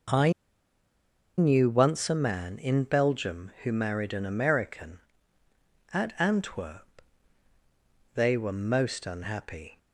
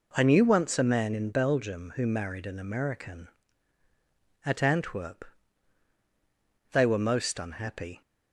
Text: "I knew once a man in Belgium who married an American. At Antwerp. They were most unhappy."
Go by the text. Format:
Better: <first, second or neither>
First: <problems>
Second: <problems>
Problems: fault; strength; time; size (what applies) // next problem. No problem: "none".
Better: second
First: pauses between "I" and "knew"; at 0.3 s; 1.0 s long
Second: none